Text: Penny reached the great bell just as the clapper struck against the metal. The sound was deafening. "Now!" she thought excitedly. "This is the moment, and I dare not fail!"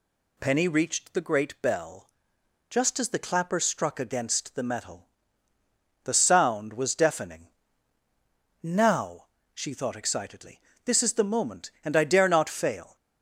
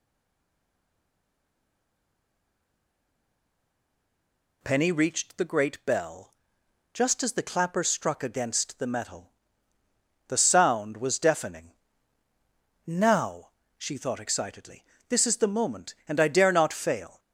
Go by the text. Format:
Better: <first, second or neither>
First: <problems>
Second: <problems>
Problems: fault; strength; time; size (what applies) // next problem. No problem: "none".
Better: first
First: pauses between "bell" and "just"; noticeable; at 2.0 s; 0.60 s long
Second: stays silent before the first word; strong; until 4.6 s; 4.6 s long // pauses between "bell" and "just"; noticeable; at 6.3 s; 0.60 s long